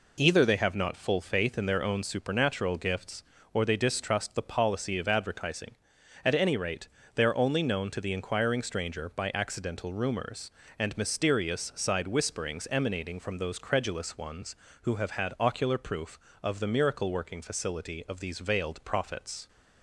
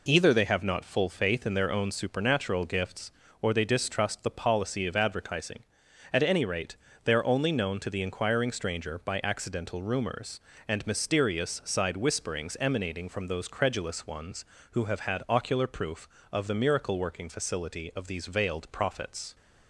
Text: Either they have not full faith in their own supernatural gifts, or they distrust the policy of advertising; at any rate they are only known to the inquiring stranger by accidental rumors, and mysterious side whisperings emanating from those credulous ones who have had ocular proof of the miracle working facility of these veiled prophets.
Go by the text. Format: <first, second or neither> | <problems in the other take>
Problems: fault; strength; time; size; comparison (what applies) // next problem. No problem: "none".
neither | pauses between "rate" and "they"; slight; the same in both